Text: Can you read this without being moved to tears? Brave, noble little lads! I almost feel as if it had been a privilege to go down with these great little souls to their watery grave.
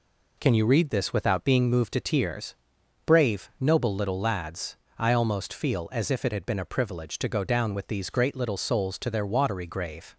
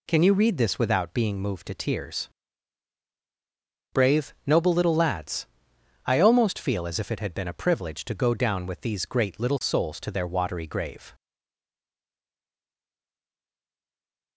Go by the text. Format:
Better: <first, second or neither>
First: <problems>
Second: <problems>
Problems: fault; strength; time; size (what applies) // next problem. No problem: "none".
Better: first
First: none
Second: stays silent after the last word; strong; from 11.1 s on; 3.2 s long